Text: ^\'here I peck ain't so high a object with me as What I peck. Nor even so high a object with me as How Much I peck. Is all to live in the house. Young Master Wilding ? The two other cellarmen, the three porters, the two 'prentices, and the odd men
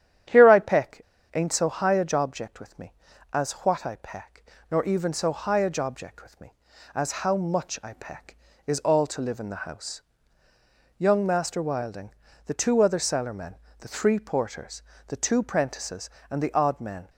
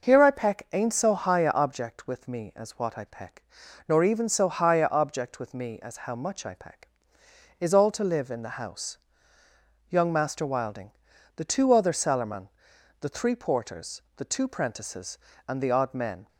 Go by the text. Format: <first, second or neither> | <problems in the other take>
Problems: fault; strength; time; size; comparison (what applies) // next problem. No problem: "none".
second | starts louder than the rest; strong; until 1.6 s; 9.5 dB // pauses between "peck" and "ain't"; slight; at 1.0 s; 0.33 s long